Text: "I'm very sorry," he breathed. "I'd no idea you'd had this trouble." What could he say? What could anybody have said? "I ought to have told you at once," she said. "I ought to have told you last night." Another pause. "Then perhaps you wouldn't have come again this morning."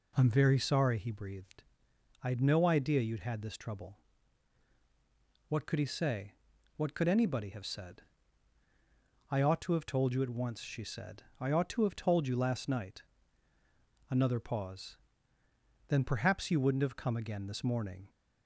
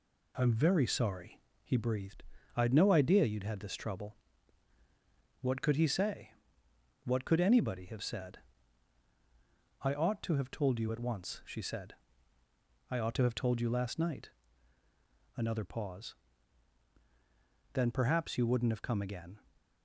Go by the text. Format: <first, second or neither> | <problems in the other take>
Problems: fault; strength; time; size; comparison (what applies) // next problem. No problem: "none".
first | stops before "this morning"; at 19.5 s